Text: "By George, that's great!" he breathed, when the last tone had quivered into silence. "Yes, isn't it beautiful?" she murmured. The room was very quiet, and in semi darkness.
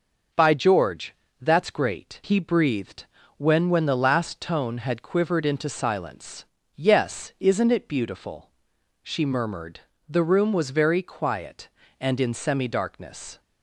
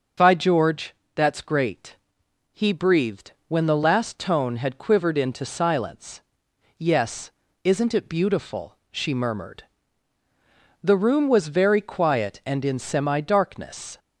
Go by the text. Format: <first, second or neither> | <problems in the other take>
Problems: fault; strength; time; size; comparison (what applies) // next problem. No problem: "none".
second | starts louder than the rest; noticeable; until 1.6 s; 6 dB // says "when" twice; at 3.6 s